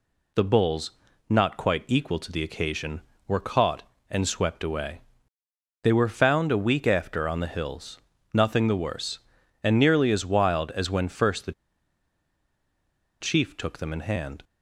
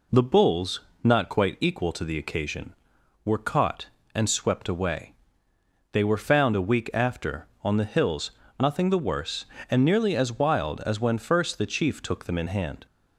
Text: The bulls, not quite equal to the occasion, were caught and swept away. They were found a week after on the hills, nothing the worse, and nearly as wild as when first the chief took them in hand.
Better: second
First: pauses between "the" and "chief"; strong; at 11.5 s; 1.6 s long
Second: none

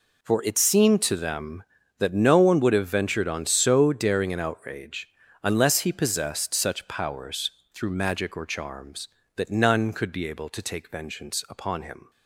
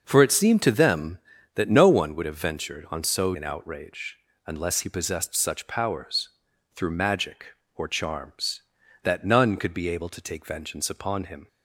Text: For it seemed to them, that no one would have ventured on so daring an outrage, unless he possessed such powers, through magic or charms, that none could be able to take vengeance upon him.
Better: first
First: none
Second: starts louder than the rest; noticeable; until 1.0 s; 6 dB // skips "daring"; at 3.3 s

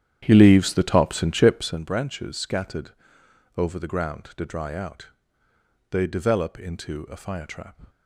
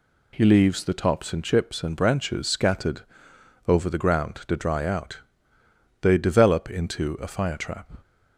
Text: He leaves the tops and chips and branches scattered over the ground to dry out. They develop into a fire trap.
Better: second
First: starts louder than the rest; strong; until 1.8 s; 10 dB // pauses between "scattered" and "over"; noticeable; at 2.9 s; 0.66 s long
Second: pauses between "scattered" and "over"; noticeable; at 3.0 s; 0.66 s long

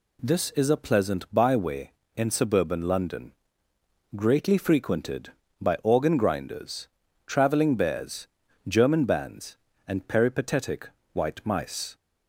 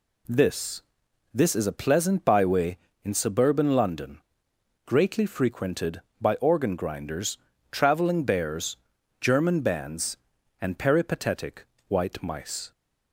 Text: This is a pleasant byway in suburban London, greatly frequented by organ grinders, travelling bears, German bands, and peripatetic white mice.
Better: first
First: pauses between "peripatetic" and "white"; slight; at 10.8 s; 0.24 s long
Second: says "This" twice; at 1.3 s // pauses between "peripatetic" and "white"; slight; at 11.6 s; 0.24 s long

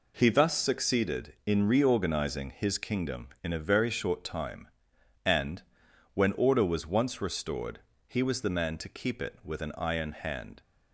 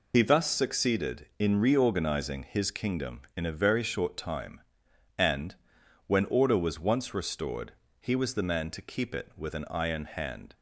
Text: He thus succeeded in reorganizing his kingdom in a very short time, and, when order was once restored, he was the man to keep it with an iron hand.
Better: first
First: none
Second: loses the start of "He"; at 0.1 s; 75 ms

